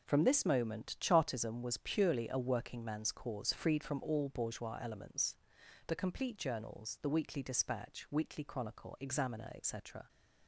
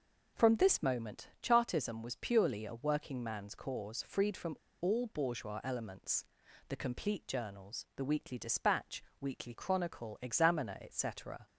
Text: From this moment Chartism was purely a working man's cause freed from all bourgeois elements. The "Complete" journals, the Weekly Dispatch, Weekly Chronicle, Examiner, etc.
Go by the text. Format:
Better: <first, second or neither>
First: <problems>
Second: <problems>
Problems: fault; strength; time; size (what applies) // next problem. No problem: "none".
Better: first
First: none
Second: pauses between "from" and "all"; slight; at 4.5 s; 0.26 s long